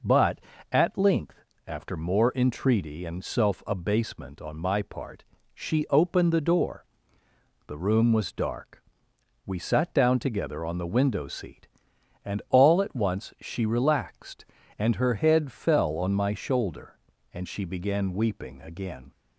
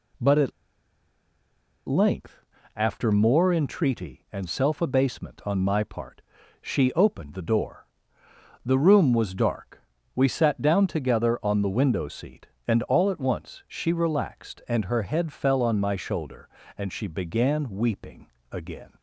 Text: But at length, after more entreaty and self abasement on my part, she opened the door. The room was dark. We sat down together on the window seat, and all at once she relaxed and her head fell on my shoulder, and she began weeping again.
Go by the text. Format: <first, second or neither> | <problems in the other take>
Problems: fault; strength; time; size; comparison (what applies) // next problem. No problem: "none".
first | pauses between "at" and "length"; strong; at 0.5 s; 1.3 s long // pauses between "weeping" and "again"; slight; at 18.2 s; 0.26 s long